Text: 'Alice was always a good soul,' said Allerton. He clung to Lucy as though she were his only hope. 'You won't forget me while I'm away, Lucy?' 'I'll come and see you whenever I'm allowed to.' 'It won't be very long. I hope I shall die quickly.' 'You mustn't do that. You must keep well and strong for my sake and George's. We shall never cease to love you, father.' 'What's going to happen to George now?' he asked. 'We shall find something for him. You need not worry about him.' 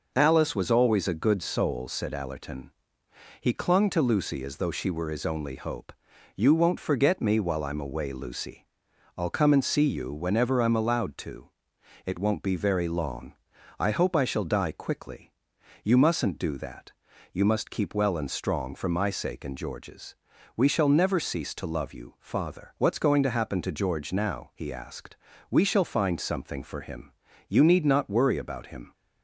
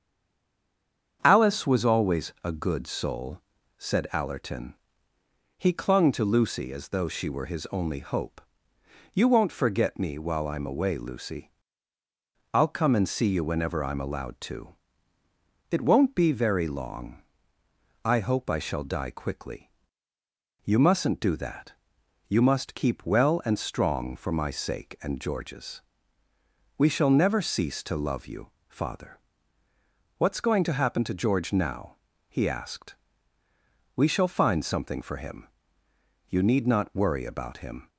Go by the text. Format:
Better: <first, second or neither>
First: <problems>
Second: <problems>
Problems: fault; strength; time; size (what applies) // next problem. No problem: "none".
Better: first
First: none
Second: stays silent before the first word; noticeable; until 1.2 s; 1.2 s long // starts louder than the rest; strong; until 2.2 s; 7.5 dB